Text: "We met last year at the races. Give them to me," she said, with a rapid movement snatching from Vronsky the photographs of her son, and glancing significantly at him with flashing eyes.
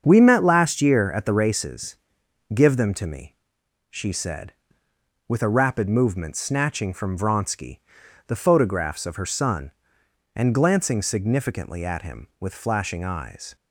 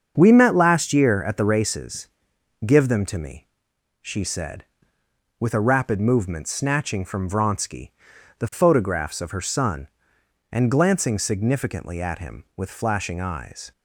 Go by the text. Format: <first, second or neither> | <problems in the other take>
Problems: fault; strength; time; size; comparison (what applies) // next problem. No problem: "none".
neither | starts louder than the rest; the same in both // pauses between "Vronsky" and "the"; noticeable; the same in both